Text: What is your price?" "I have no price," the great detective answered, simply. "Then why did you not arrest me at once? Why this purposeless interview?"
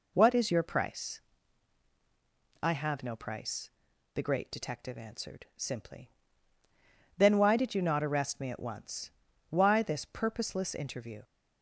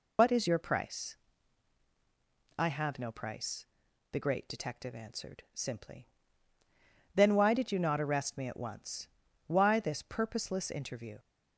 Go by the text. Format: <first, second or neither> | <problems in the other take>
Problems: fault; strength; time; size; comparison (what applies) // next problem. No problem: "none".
first | loses the start of "What"; at 0.1 s; 75 ms